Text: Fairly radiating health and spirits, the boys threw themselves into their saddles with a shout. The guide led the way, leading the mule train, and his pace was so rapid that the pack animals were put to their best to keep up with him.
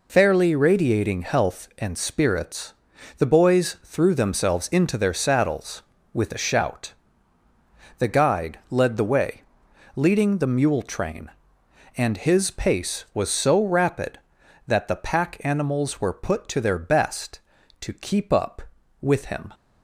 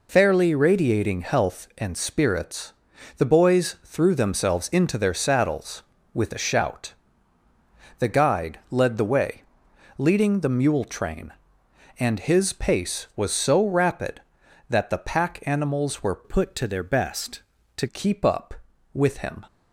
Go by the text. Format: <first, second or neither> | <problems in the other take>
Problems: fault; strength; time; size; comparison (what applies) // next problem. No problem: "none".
first | changes voice from "put" to "to"; from 16.2 to 17.8 s; 1.6 s long